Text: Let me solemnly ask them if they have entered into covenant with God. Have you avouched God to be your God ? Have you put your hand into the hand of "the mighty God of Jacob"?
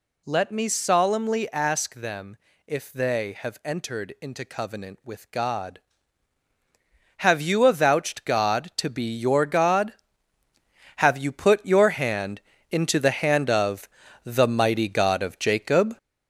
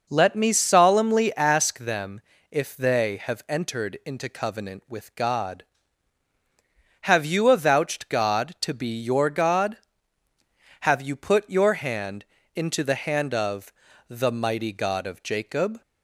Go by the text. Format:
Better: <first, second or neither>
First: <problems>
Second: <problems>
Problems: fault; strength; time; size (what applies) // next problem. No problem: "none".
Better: second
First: gets louder; noticeable; throughout; 5 dB // pauses between "them" and "if"; slight; at 2.3 s; 0.28 s long // pauses between "hand" and "into"; slight; at 12.3 s; 0.32 s long // pauses between "of" and "the"; slight; at 13.8 s; 0.34 s long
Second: pauses between "them" and "if"; slight; at 2.2 s; 0.28 s long // pauses between "hand" and "into"; slight; at 12.2 s; 0.32 s long // pauses between "of" and "the"; slight; at 13.7 s; 0.34 s long